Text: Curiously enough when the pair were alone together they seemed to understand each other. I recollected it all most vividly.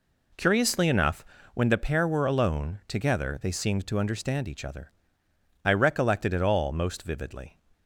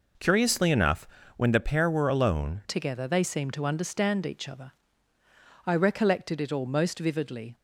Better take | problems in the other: first | pauses between "enough" and "when"; slight; at 1.0 s; 0.30 s long; slight in the first // changes voice at "together"; from 2.6 s on; 4.9 s long

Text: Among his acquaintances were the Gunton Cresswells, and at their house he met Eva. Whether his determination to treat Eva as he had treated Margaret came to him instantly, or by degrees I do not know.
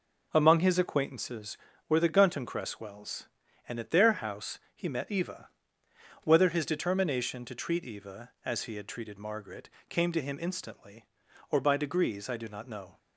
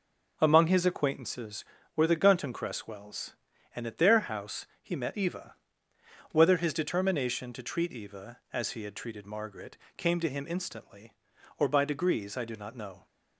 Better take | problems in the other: neither | pauses between "house" and "he"; slight; the same in both // pauses between "Margaret" and "came"; slight; the same in both

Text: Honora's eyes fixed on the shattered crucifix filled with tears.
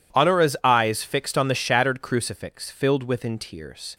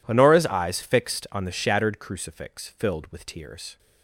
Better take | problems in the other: second | says "within" for "with"; at 3.0 s

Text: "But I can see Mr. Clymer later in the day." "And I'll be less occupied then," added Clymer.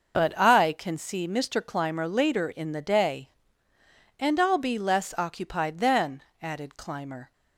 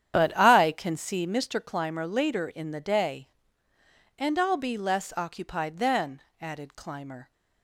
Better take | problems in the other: first | starts louder than the rest; strong; until 1.5 s; 9.5 dB

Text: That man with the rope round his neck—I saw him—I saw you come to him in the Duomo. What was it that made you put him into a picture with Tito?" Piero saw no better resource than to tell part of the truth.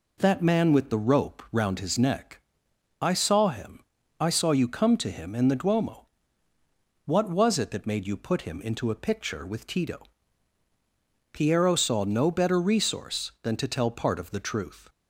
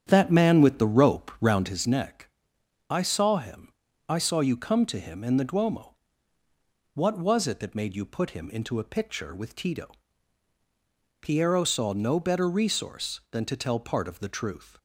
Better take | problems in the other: first | starts louder than the rest; strong; until 1.8 s; 9 dB

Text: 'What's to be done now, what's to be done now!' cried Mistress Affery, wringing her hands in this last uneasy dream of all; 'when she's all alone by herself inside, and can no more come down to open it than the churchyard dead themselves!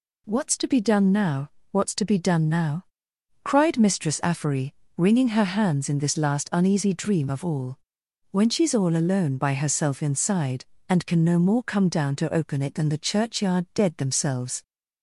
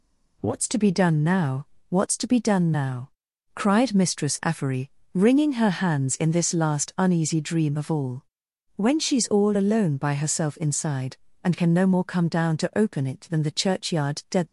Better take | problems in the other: first | stops before "themselves"; at 14.4 s

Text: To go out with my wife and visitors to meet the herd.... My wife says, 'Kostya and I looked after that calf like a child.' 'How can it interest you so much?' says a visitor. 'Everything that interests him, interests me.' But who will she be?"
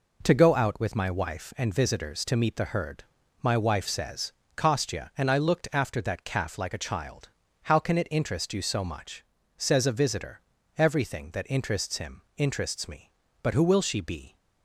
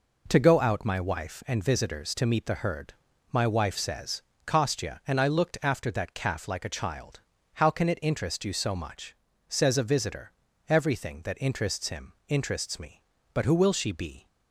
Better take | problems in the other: first | skips "with"; at 0.8 s

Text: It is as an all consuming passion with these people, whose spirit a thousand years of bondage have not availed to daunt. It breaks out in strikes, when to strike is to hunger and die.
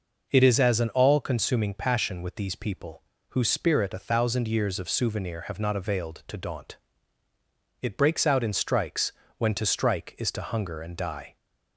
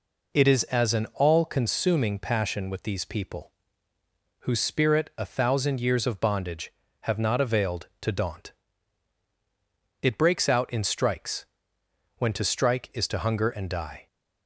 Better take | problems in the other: second | says "souvenir" for "bondage"; at 4.8 s

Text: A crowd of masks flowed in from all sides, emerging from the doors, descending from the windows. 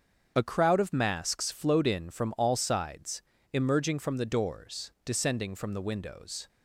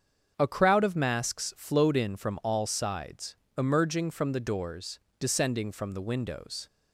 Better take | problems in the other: neither | starts louder than the rest; the same in both

